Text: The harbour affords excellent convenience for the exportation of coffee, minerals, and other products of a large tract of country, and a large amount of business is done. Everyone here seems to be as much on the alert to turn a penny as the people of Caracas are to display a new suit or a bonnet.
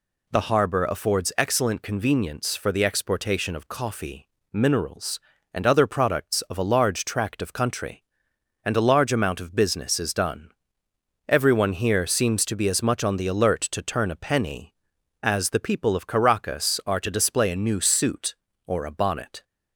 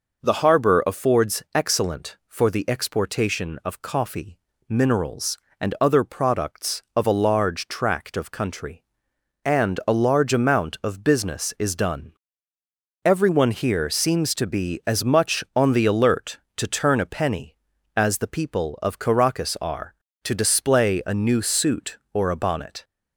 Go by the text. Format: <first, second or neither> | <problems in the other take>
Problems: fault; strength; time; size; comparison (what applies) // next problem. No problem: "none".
first | skips "convenience"; at 2.2 s